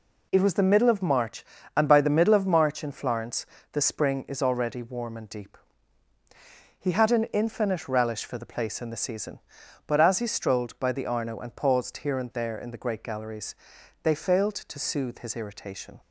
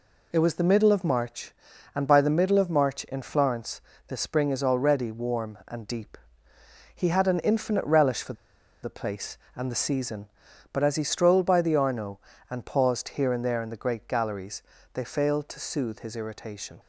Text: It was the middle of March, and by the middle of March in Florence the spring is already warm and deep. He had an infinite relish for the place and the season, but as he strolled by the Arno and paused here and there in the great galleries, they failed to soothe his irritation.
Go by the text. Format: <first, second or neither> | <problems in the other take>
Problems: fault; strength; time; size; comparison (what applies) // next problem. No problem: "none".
first | pauses between "Florence" and "the"; slight; at 3.8 s; 0.28 s long; slight in the first // pauses between "for" and "the"; noticeable; at 8.3 s; 0.49 s long